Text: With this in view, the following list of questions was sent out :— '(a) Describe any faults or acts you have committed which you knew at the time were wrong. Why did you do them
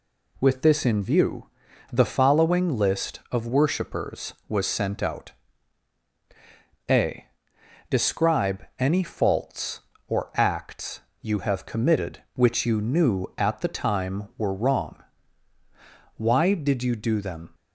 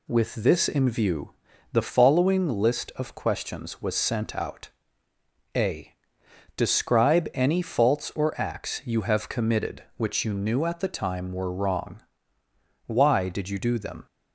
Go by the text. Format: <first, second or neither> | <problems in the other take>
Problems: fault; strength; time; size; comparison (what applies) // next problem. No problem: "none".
second | says "worshipers" for "questions"; at 3.4 s // pauses between "acts" and "you"; slight; at 11.0 s; 0.20 s long